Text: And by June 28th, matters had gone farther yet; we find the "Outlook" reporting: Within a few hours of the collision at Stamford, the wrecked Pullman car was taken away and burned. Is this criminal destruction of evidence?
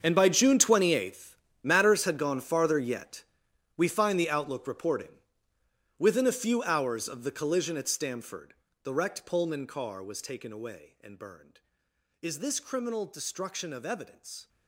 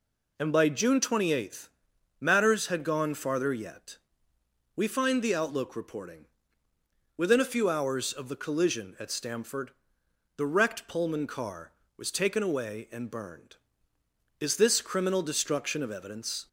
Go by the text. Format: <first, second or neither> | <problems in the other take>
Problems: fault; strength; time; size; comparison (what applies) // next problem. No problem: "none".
second | gets quieter; strong; throughout; 15.5 dB